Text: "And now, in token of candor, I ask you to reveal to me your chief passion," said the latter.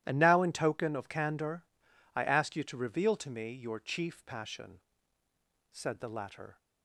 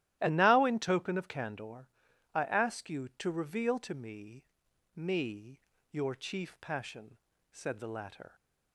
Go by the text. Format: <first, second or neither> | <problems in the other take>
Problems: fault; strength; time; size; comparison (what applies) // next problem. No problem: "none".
first | starts louder than the rest; strong; until 1.2 s; 14 dB; strong in the first // says "me" twice; at 4.9 s